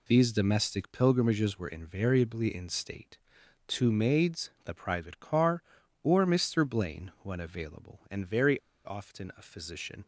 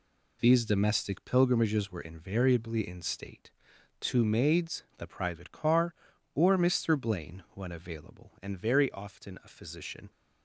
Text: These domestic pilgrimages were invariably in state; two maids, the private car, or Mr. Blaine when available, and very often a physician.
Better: second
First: pauses between "very" and "often"; slight; at 8.5 s; 0.25 s long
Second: none

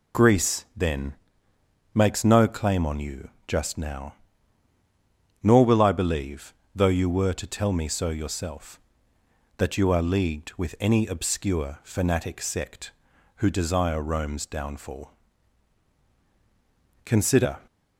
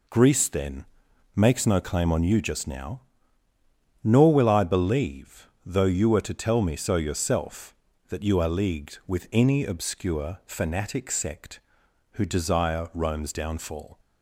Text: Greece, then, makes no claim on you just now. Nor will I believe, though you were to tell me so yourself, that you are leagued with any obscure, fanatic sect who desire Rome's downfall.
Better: second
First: pauses between "you" and "just"; slight; at 3.2 s; 0.20 s long // goes on to say "Consider"; from 17.0 s on; 0.54 s long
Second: none

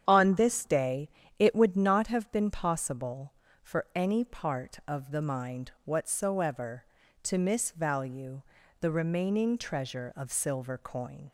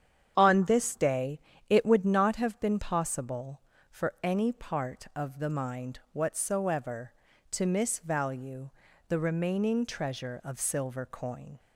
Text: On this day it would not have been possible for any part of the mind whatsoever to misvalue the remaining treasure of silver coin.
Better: neither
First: starts louder than the rest; strong; until 1.0 s; 8.5 dB // pauses between "day" and "it"; slight; at 1.0 s; 0.30 s long // pauses between "misvalue" and "the"; at 8.4 s; 0.38 s long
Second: starts louder than the rest; strong; until 1.3 s; 8.5 dB // pauses between "day" and "it"; slight; at 1.3 s; 0.30 s long // pauses between "misvalue" and "the"; at 8.7 s; 0.38 s long

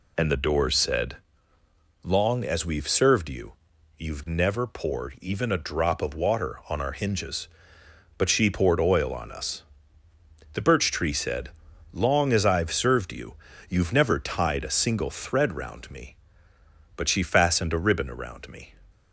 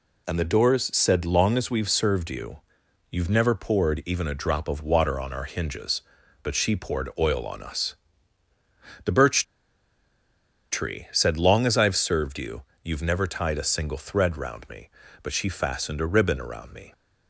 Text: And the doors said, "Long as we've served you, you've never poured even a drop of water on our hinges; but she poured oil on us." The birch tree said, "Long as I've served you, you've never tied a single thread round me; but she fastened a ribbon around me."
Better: first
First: none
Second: pauses between "birch" and "tree"; strong; at 9.4 s; 1.2 s long

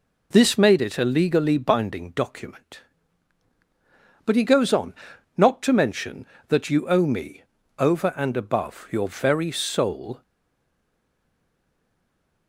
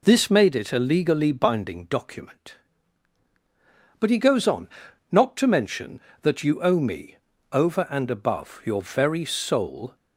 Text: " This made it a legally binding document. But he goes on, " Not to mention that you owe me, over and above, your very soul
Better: second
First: stays silent after the last word; from 10.2 s on; 2.2 s long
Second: none

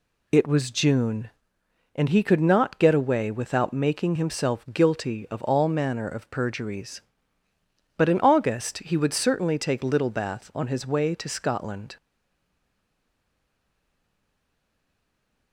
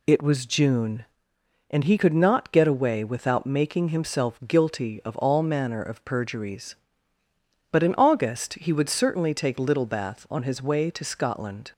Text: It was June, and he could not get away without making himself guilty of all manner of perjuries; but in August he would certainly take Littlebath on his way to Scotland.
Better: second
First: stays silent after the last word; strong; from 11.9 s on; 3.6 s long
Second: none

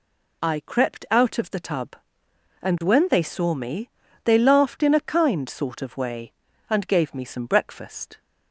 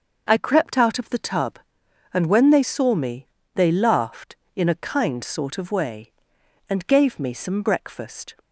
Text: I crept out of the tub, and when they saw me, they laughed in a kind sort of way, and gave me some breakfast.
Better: neither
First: none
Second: none

